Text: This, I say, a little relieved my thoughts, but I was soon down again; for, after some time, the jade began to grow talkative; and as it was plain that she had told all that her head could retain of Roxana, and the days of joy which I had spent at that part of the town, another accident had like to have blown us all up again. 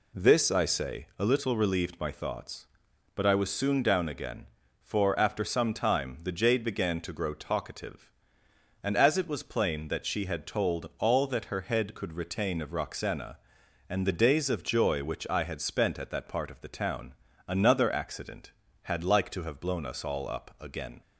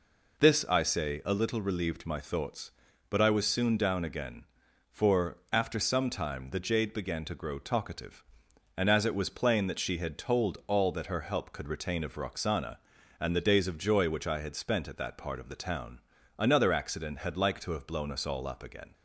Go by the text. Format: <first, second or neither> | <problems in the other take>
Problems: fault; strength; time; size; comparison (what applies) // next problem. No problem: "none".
first | says "help" for "head"; at 11.2 s